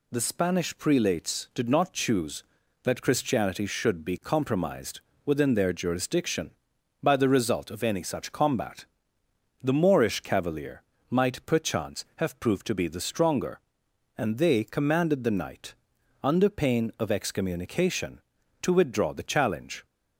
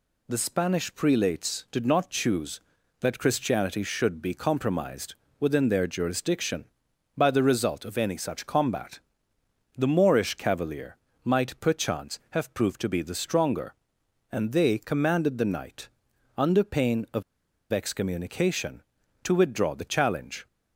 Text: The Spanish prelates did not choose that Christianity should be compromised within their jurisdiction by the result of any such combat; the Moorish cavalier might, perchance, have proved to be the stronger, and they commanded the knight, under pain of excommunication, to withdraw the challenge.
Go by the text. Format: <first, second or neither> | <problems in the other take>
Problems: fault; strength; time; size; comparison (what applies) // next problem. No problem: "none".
first | pauses between "compromised" and "within"; slight; at 5.1 s; 0.26 s long; slight in the first // pauses between "cavalier" and "might"; slight; at 10.9 s; 0.26 s long; slight in the first // pauses between "of" and "excommunication"; noticeable; at 17.2 s; 0.47 s long